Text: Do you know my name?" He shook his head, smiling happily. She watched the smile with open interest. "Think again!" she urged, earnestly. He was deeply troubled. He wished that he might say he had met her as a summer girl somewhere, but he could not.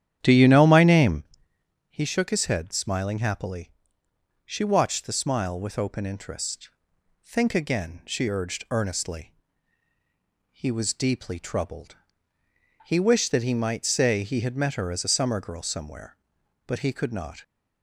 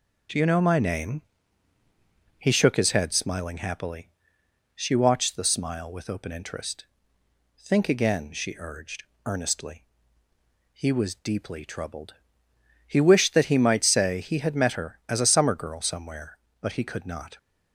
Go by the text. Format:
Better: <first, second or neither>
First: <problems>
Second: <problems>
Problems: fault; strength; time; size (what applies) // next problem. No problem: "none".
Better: second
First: starts louder than the rest; strong; until 1.3 s; 10 dB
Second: none